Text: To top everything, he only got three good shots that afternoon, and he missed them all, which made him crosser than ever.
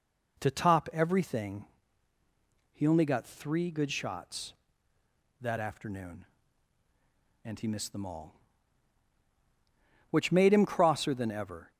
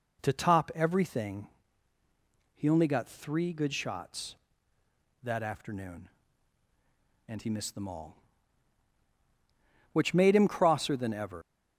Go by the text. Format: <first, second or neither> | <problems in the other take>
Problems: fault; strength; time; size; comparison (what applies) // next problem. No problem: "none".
first | leaves "ever" unfinished; at 11.4 s; 115 ms